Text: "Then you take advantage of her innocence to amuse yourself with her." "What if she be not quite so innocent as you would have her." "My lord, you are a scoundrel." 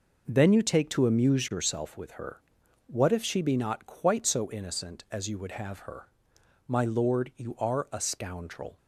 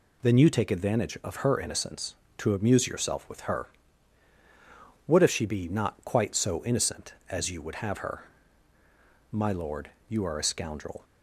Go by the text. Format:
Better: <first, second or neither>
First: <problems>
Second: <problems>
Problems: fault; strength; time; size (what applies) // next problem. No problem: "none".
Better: second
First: skips "advantage of her innocence"; at 0.8 s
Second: none